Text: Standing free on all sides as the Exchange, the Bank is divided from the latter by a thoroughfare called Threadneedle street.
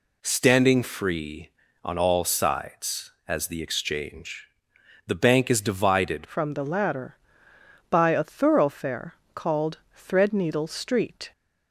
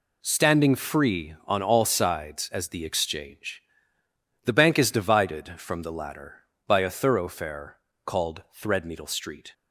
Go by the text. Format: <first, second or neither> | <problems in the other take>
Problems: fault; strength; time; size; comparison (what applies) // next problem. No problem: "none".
second | changes voice at "from"; from 6.2 s on; 5.1 s long // pauses between "thoroughfare" and "called"; slight; at 9.1 s; 0.18 s long; slight in the second